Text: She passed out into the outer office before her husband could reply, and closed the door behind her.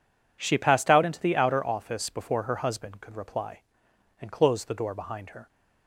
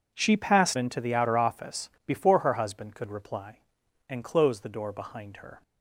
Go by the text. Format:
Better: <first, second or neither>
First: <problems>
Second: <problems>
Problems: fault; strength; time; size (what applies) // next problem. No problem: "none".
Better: first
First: none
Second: skips "out"; at 0.7 s // pauses between "office" and "before"; slight; at 1.8 s; 0.16 s long